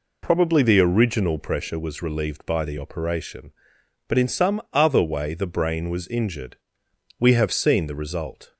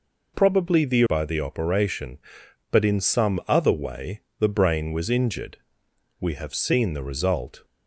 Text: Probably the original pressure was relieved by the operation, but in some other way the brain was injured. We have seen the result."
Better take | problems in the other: first | skips "original pressure was relieved"; at 1.0 s // pauses between "way" and "the"; slight; at 4.2 s; 0.18 s long

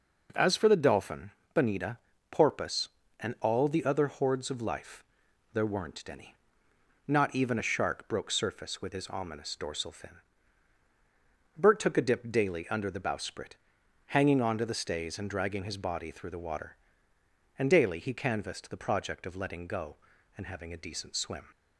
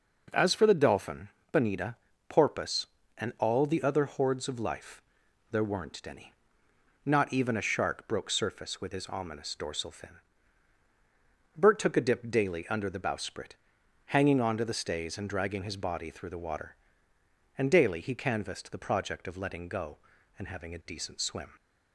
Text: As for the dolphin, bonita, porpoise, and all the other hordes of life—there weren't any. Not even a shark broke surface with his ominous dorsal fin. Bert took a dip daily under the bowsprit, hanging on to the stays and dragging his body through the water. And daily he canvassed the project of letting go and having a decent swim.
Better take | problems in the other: neither | none

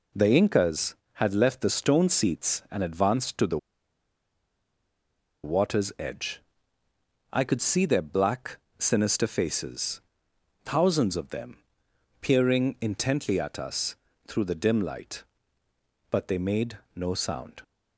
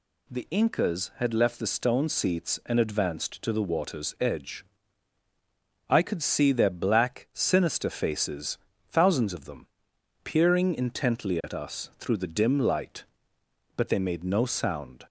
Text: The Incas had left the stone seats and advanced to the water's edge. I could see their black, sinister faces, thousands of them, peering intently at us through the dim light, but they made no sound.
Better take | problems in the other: second | pauses between "the" and "water's"; strong; at 3.5 s; 1.8 s long // pauses between "us" and "through"; slight; at 13.9 s; 0.32 s long // pauses between "made" and "no"; slight; at 16.7 s; 0.18 s long

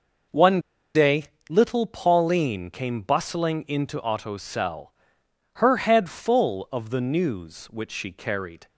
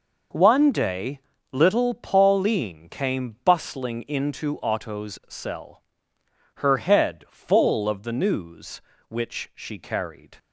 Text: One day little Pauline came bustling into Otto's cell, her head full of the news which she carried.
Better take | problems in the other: second | pauses between "One" and "day"; slight; at 0.6 s; 0.34 s long // pauses between "day" and "little"; slight; at 1.2 s; 0.26 s long; slight in the second

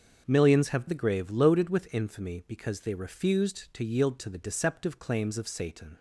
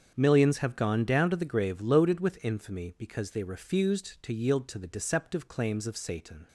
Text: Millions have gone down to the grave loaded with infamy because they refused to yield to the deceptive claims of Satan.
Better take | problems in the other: second | starts louder than the rest; until 1.2 s; 7 dB; strong in the second // skips "gone down to"; at 0.8 s

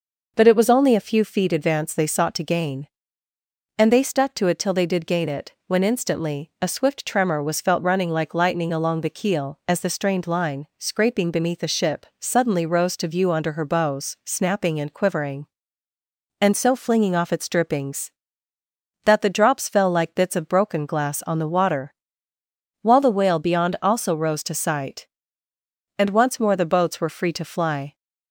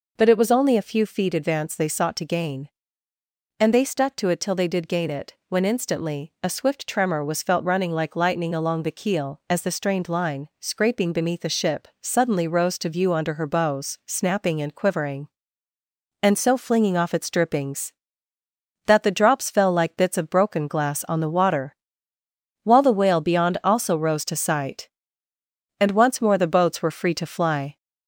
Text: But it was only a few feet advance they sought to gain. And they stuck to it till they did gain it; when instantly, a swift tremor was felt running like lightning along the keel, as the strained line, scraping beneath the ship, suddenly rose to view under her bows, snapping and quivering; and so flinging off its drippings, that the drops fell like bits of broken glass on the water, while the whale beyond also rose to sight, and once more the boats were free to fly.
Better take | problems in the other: first | gets louder; slight; throughout; 2.5 dB

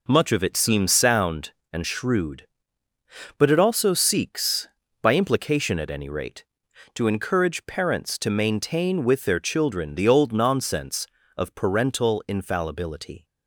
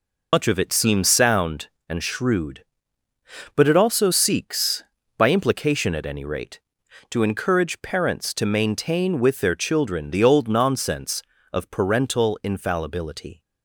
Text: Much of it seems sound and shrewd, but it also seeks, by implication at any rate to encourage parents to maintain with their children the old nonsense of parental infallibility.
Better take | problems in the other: first | loses the start of "Much"; at 0.3 s; 95 ms

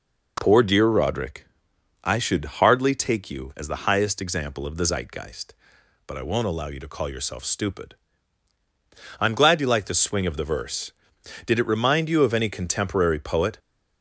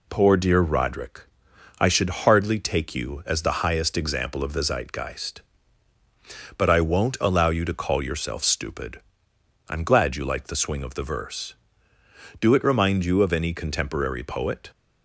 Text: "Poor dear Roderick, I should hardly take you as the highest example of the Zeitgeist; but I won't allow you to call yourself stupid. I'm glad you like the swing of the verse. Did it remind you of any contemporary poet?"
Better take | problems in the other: first | says "Do" for "Did"; at 12.3 s

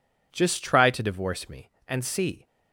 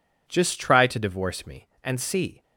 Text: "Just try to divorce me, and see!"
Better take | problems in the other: neither | none

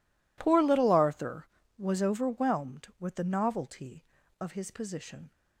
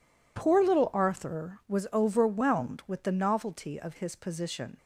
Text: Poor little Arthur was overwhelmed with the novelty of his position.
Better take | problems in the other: neither | none

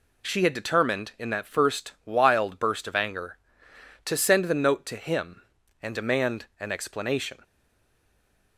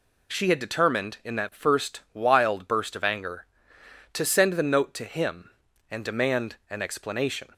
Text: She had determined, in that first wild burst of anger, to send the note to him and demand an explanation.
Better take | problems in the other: second | pauses between "demand" and "an"; slight; at 6.4 s; 0.16 s long; slight in the second // stays silent after the last word; from 7.4 s on; 1.1 s long

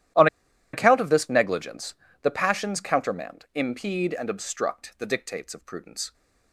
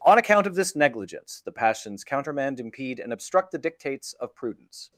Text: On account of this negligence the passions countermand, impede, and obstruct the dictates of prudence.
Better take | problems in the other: second | starts louder than the rest; strong; until 1.6 s; 12.5 dB // pauses between "On" and "account"; noticeable; at 0.2 s; 0.46 s long // pauses between "negligence" and "the"; slight; at 1.9 s; 0.28 s long

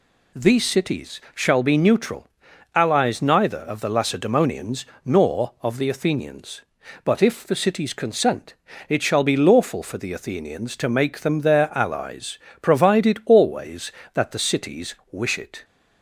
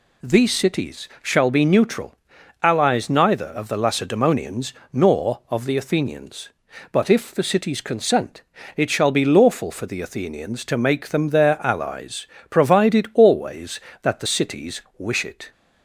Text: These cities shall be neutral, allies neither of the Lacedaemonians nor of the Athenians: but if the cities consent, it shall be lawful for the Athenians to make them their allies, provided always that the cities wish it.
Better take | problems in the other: neither | pauses between "cities" and "shall"; slight; the same in both // pauses between "Lacedaemonians" and "nor"; slight; the same in both // pauses between "cities" and "wish"; slight; the same in both

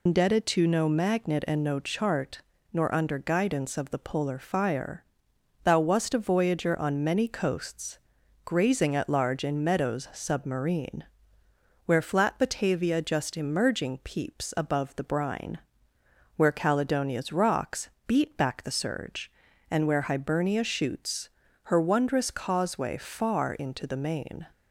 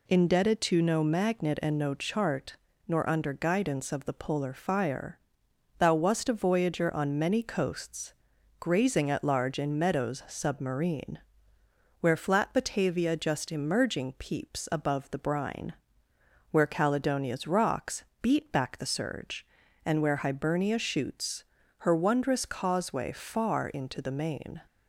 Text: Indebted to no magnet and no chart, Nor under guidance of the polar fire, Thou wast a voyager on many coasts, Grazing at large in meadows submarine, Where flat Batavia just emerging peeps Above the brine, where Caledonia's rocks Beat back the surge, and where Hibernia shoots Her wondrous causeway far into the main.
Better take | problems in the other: second | loses the start of "Indebted"; at 0.0 s; 125 ms // pauses between "rocks" and "Beat"; slight; at 17.8 s; 0.18 s long; slight in the second // pauses between "shoots" and "Her"; slight; at 21.2 s; 0.34 s long; slight in the second

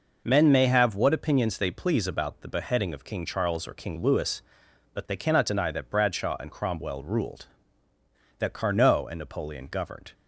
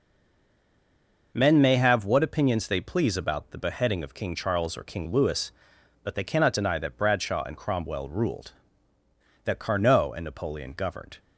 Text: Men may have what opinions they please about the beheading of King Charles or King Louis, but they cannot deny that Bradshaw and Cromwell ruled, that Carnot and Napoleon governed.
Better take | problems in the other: first | stays silent before the first word; noticeable; until 1.3 s; 1.3 s long

